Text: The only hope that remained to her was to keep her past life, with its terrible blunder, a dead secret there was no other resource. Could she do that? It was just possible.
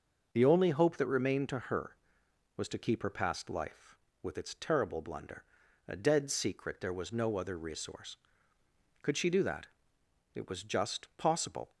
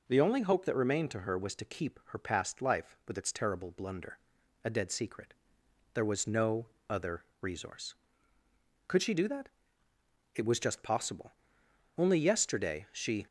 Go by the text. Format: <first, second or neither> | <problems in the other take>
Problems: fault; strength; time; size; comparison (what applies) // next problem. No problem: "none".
first | pauses between "secret" and "there"; noticeable; at 5.3 s; 0.62 s long // pauses between "no" and "other"; slight; at 6.6 s; 0.24 s long // pauses between "other" and "resource"; slight; at 7.2 s; 0.16 s long // goes on to say "Only yesterday she"; noticeable; from 11.9 s on; 1.3 s long